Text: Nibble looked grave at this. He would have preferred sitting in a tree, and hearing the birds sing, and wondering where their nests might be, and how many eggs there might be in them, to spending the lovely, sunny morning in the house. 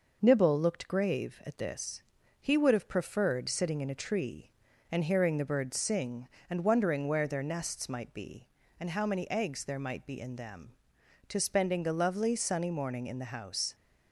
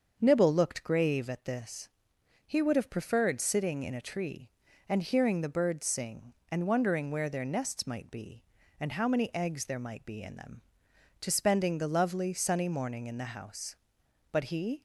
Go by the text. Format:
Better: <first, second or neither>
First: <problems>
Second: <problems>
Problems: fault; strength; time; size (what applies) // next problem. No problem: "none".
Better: first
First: none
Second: starts louder than the rest; until 1.2 s; 7 dB // goes on to say "But he"; from 14.3 s on; 0.50 s long